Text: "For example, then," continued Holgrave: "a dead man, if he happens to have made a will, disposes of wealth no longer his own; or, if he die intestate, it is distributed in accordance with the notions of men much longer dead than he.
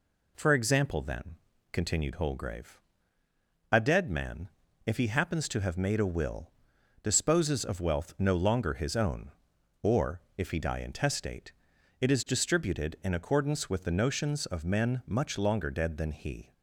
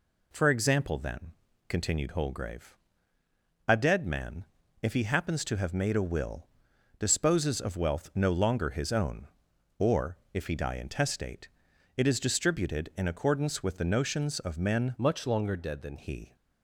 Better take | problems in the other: first | changes voice from "much" to "than"; from 14.9 to 15.9 s; 1.0 s long

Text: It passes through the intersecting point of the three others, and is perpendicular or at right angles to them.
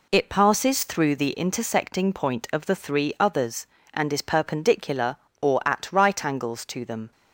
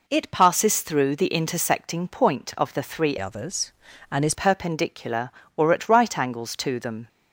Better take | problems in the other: first | changes voice from "others" to "is"; from 3.1 to 4.3 s; 1.2 s long

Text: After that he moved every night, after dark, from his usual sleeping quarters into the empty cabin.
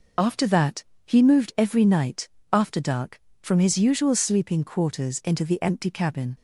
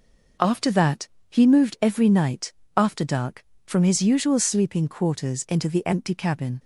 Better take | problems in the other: second | loses the start of "After"; at 0.1 s; 25 ms // pauses between "that" and "he"; slight; at 0.8 s; 0.22 s long; slight in the second

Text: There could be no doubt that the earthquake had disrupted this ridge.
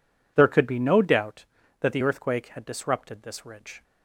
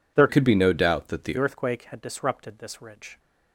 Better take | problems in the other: first | changes voice from "could" to "the"; from 0.2 to 1.3 s; 1.1 s long

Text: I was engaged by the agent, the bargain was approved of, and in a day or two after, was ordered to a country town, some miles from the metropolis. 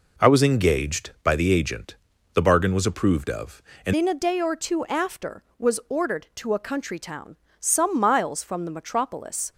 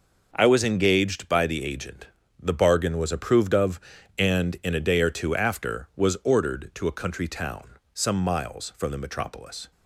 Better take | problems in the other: second | changes voice at "in"; from 3.9 s on; 5.6 s long

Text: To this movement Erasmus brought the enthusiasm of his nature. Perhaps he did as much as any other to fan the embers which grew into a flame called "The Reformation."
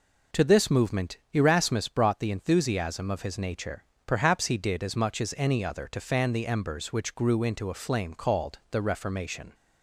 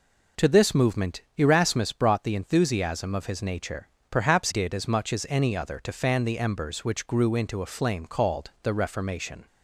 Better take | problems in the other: first | pauses between "movement" and "Erasmus"; slight; at 1.2 s; 0.16 s long; slight in the first // skips "he"; at 4.4 s

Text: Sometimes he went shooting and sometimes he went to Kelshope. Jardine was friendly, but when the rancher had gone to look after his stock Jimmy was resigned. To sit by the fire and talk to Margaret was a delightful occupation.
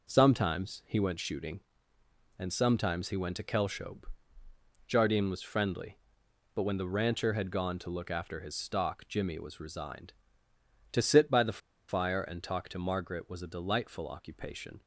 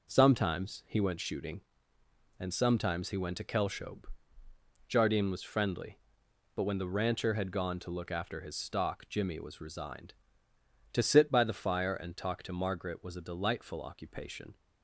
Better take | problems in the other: second | pauses between "the" and "fire"; slight; at 11.5 s; 0.29 s long

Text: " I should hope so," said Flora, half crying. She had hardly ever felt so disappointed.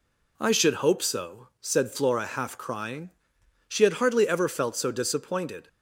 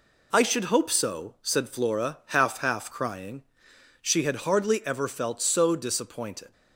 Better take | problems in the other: first | says "half" twice; at 2.5 s

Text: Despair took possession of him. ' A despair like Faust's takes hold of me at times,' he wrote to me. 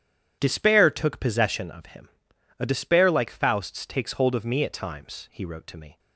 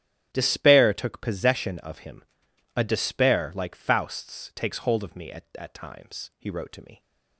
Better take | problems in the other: first | starts louder than the rest; strong; until 1.3 s; 10 dB; strong in the first // says "at" twice; at 5.5 s

